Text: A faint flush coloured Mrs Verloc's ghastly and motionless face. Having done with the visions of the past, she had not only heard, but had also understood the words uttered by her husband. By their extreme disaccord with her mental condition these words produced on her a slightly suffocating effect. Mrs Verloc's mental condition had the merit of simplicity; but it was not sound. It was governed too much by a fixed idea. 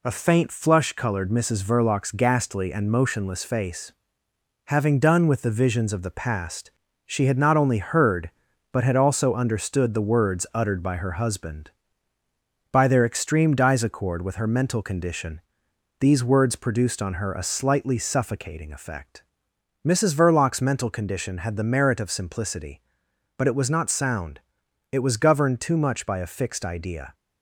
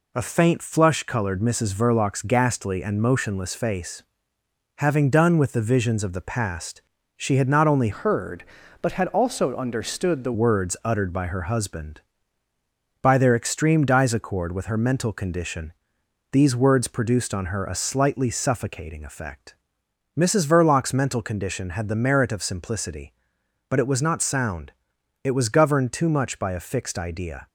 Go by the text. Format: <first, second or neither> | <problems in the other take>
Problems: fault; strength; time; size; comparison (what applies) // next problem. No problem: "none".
first | changes voice from "heard" to "the"; from 7.9 to 10.3 s; 2.4 s long // pauses between "condition" and "these"; noticeable; at 15.7 s; 0.58 s long; noticeable in the first